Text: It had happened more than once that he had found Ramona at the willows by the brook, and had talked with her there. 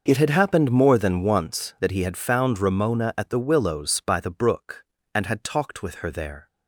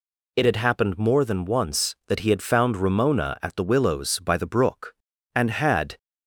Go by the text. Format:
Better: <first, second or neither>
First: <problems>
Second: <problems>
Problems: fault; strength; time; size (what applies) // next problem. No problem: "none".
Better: first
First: none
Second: stops before "talked with her there"; at 5.9 s